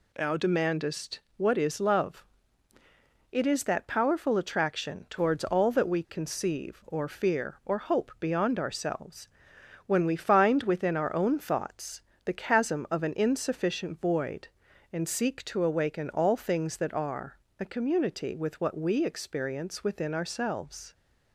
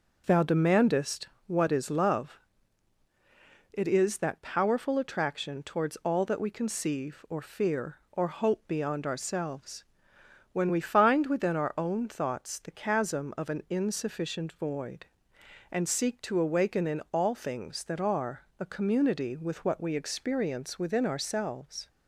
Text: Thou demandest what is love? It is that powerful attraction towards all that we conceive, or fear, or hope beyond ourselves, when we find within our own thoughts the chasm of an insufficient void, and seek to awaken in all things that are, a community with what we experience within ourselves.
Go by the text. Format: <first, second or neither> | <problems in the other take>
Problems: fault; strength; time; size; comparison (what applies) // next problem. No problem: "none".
second | pauses between "demandest" and "what"; slight; at 1.2 s; 0.18 s long; slight in the second // pauses between "thoughts" and "the"; slight; at 12.0 s; 0.24 s long // skips "in"; at 16.0 s